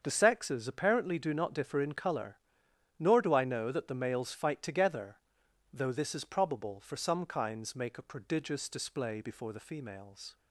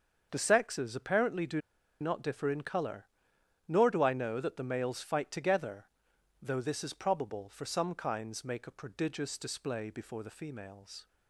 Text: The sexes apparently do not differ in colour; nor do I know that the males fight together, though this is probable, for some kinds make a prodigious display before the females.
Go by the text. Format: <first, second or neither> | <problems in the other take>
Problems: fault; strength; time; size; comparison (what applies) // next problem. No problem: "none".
first | starts louder than the rest; until 1.3 s; 6.5 dB; also in the first // pauses between "do" and "not"; at 1.5 s; 0.41 s long